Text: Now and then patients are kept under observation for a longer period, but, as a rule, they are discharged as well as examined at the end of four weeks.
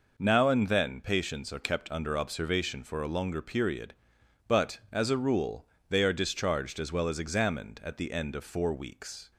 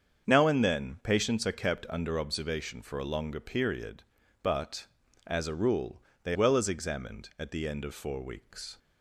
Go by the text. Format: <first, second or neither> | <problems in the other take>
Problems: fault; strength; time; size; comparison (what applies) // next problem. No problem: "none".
first | starts louder than the rest; strong; until 1.3 s; 7 dB // skips "are discharged as"; at 6.3 s